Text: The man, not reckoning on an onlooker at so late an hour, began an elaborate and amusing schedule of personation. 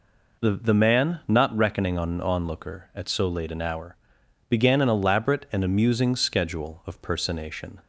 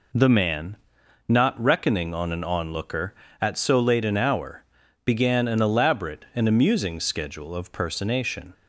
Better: second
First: says "The" twice; at 0.5 s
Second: none

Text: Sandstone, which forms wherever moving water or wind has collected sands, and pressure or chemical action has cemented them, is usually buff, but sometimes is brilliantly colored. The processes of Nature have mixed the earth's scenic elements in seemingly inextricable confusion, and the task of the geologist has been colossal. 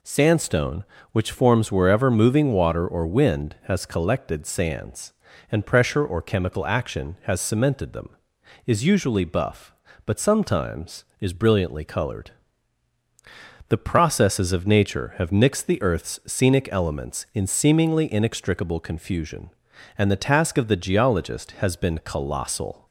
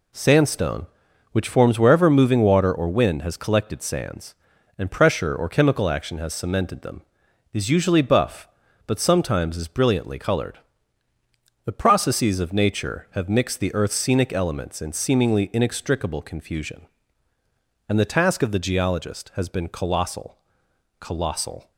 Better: first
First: none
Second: says "colossal" twice; at 20.9 s

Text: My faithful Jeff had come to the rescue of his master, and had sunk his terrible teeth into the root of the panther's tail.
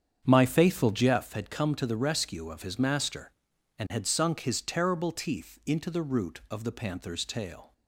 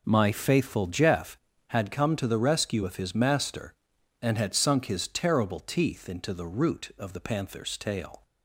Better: second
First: starts louder than the rest; strong; until 1.3 s; 8 dB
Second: none

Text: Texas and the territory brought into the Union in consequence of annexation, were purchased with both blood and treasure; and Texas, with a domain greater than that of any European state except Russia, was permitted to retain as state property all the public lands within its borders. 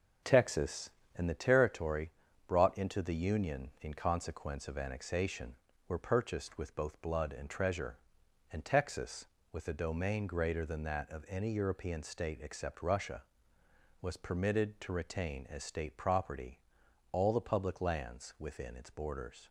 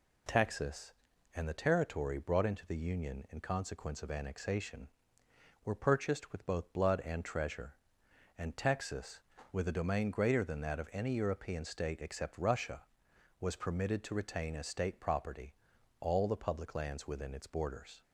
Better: second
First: starts louder than the rest; until 1.2 s; 6.5 dB // pauses between "territory" and "brought"; at 2.0 s; 0.38 s long // pauses between "property" and "all"; noticeable; at 16.5 s; 0.52 s long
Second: pauses between "property" and "all"; noticeable; at 15.5 s; 0.48 s long

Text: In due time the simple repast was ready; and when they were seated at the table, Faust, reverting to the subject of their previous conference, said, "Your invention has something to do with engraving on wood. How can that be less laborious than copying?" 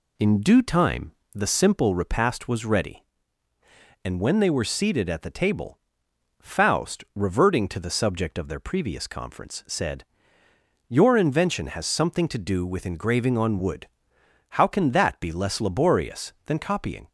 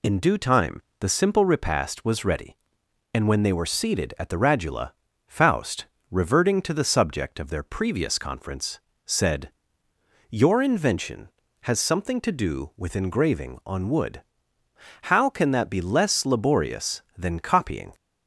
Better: first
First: pauses between "time" and "the"; slight; at 1.1 s; 0.22 s long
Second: pauses between "time" and "the"; slight; at 0.8 s; 0.20 s long // says "radula" for "table"; at 4.3 s

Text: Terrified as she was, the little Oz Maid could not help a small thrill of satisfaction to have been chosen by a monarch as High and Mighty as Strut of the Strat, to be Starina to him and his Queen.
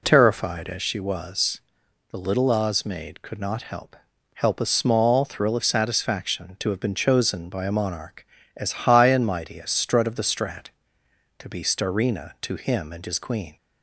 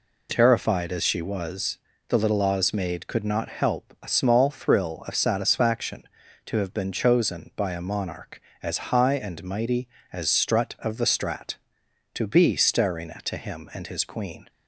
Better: second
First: says "help" twice; at 4.3 s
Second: none

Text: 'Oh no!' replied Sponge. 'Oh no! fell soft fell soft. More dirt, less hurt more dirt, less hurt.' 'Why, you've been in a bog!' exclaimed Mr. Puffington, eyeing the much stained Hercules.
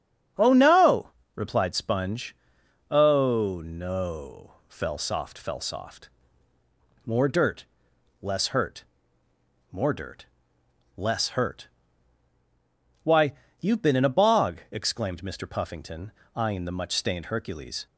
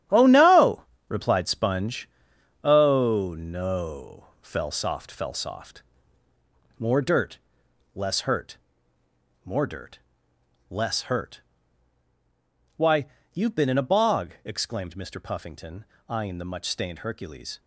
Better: first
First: starts louder than the rest; strong; until 1.6 s; 8.5 dB // pauses between "hurt" and "more"; noticeable; at 8.8 s; 0.86 s long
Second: gets quieter; strong; throughout; 10 dB // starts louder than the rest; strong; until 1.3 s; 10.5 dB // pauses between "hurt" and "more"; noticeable; at 8.5 s; 0.86 s long

